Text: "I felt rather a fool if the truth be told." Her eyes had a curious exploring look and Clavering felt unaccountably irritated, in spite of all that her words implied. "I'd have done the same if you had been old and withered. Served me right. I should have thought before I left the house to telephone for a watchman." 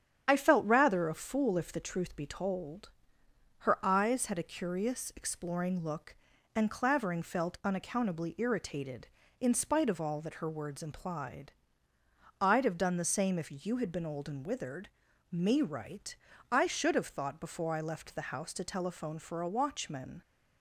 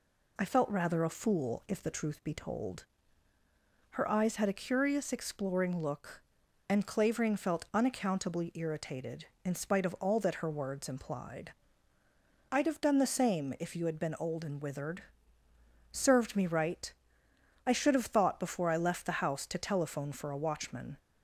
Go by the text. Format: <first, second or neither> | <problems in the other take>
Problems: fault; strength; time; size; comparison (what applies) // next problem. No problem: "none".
second | starts louder than the rest; strong; until 1.2 s; 8.5 dB // skips "Served"; at 15.0 s